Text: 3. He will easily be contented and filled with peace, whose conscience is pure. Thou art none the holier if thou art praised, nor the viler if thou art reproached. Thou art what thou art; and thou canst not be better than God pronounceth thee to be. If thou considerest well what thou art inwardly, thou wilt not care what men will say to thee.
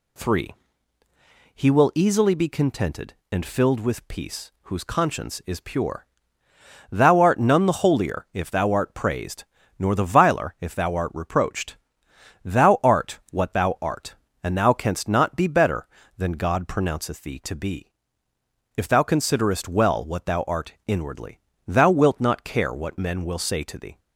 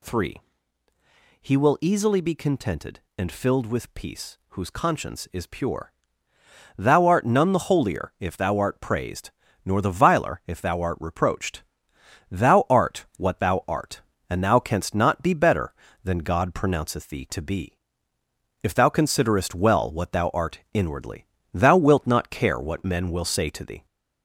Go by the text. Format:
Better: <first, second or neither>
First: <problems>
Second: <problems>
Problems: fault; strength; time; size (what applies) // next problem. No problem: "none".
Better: first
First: none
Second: gets louder; slight; throughout; 2.5 dB